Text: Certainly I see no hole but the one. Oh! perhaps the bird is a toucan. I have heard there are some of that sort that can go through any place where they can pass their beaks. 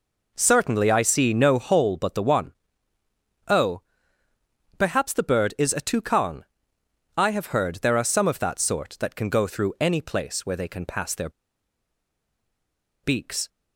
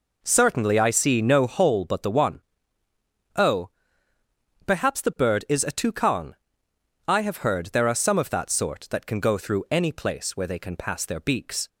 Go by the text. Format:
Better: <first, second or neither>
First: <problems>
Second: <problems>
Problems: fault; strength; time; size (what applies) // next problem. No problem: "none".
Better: second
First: pauses between "their" and "beaks"; strong; at 11.2 s; 1.7 s long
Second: none